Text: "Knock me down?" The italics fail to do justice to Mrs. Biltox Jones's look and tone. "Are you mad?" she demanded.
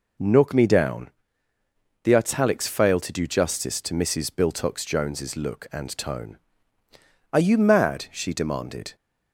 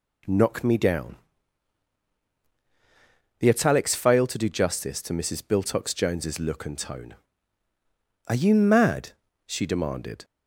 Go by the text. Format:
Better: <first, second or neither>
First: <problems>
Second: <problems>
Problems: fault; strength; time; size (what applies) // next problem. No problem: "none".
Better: neither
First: none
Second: none